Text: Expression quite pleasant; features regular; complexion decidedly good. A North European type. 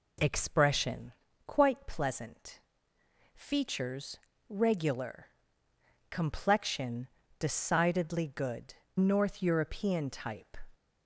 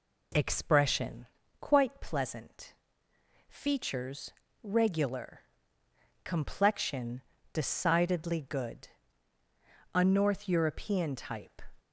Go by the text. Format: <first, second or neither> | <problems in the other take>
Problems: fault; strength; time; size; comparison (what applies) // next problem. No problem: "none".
second | pauses between "Expression" and "quite"; slight; at 1.1 s; 0.34 s long; slight in the second // pauses between "features" and "regular"; slight; at 4.1 s; 0.32 s long; slight in the second // pauses between "complexion" and "decidedly"; slight; at 7.0 s; 0.32 s long; slight in the second // skips "A"; at 8.8 s